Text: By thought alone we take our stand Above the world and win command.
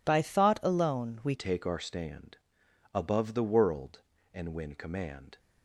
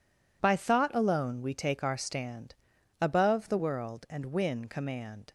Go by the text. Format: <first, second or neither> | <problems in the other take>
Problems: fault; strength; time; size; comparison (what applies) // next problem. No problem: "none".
second | changes voice at "take"; from 1.3 s on; 4.0 s long // pauses between "stand" and "Above"; noticeable; at 2.3 s; 0.56 s long; noticeable in the second